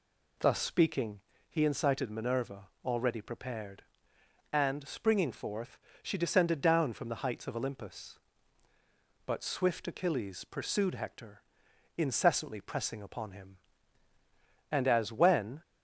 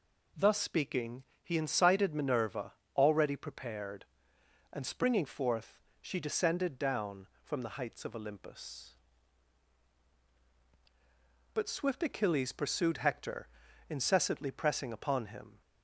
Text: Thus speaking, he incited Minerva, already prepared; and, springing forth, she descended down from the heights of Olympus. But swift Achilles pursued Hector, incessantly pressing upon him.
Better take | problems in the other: second | goes on to say "And as when"; noticeable; from 14.7 s on; 0.90 s long

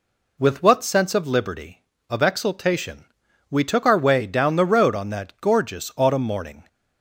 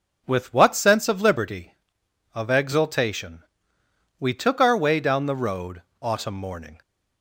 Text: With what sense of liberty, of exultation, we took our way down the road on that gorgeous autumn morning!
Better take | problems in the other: first | skips "on that gorgeous"; at 5.9 s

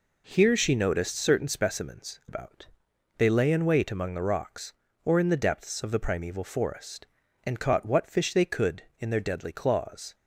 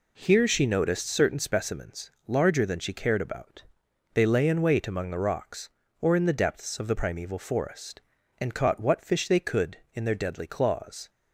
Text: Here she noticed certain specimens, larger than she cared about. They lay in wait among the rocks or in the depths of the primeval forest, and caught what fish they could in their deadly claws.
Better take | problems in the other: second | skips "larger than she cared"; at 2.2 s

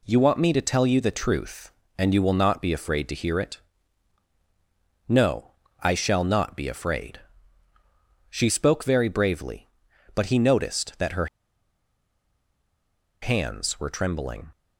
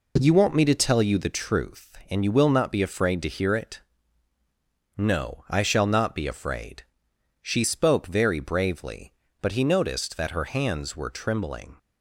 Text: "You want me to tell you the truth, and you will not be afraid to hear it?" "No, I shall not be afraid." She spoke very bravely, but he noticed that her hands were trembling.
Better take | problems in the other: second | pauses between "her" and "hands"; strong; at 11.2 s; 1.9 s long

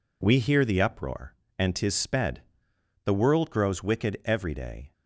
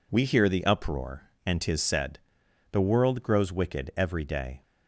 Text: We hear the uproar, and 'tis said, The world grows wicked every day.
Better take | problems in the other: second | says "sped" for "said"; at 1.9 s

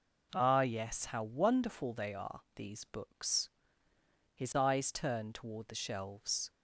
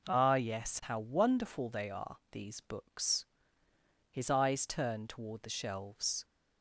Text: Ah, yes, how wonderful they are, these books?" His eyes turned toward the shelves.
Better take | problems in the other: neither | none

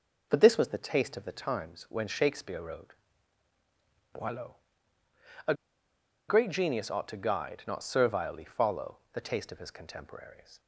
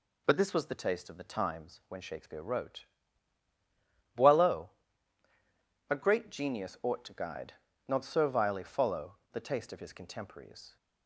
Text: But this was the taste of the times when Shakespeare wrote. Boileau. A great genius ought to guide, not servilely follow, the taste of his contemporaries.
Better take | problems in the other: second | pauses between "A" and "great"; noticeable; at 5.5 s; 0.75 s long

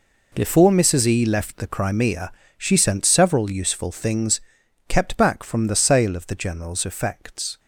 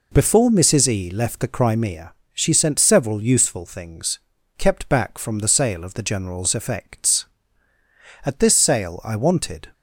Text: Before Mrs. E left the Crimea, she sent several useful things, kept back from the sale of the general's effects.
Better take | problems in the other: first | goes on to say "At this sale I wanted"; from 8.2 s on; 1.5 s long

